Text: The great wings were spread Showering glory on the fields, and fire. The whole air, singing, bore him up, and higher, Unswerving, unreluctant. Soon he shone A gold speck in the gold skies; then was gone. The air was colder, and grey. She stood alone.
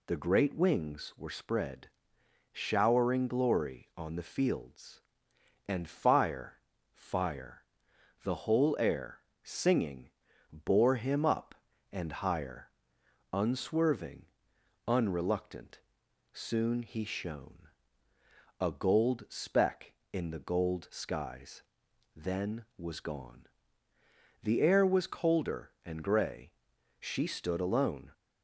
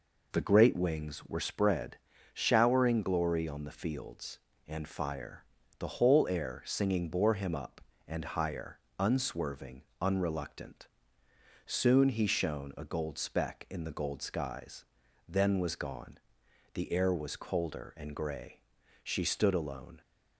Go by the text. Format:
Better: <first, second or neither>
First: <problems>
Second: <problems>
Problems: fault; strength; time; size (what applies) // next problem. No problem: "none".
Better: second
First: pauses between "spread" and "Showering"; noticeable; at 1.8 s; 0.64 s long // says "fire" twice; at 6.9 s // pauses between "shone" and "A"; noticeable; at 17.6 s; 0.92 s long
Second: pauses between "spread" and "Showering"; at 1.9 s; 0.36 s long